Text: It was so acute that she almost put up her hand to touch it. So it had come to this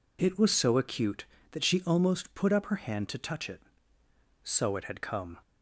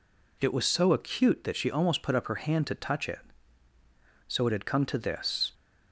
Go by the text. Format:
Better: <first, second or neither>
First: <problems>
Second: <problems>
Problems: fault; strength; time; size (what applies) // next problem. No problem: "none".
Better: second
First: stops before "to this"; at 5.4 s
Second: none